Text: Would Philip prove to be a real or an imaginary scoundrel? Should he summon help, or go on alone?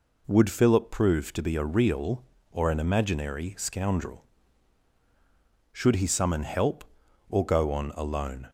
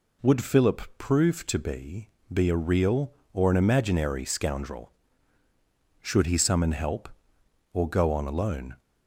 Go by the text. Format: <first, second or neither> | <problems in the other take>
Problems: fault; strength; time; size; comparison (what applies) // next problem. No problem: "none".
first | pauses between "Philip" and "prove"; slight; at 0.8 s; 0.18 s long // says "be" twice; at 2.3 s